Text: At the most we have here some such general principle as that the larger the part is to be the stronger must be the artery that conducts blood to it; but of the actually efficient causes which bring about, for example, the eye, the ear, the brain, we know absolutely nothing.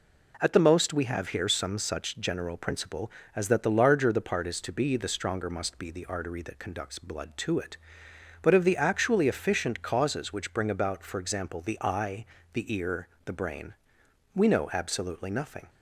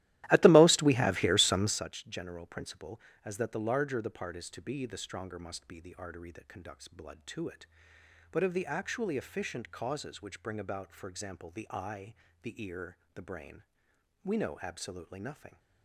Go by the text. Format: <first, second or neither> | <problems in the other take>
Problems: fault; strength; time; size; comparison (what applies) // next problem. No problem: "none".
first | starts louder than the rest; strong; until 1.8 s; 15 dB